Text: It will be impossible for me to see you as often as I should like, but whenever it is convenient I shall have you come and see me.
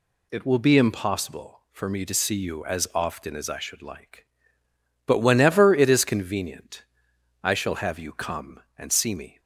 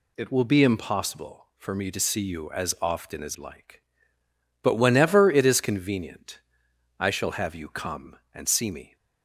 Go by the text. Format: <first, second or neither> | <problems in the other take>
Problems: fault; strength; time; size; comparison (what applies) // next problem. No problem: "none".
first | skips "I should"; at 3.3 s // pauses between "convenient" and "I"; noticeable; at 6.3 s; 0.58 s long; noticeable in the first